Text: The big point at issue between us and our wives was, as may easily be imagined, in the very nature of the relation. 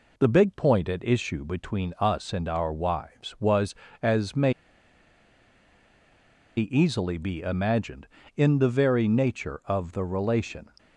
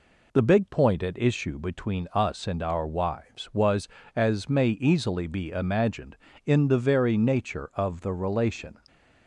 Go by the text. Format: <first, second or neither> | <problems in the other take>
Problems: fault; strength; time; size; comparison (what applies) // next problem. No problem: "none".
second | pauses between "may" and "easily"; strong; at 4.5 s; 2.0 s long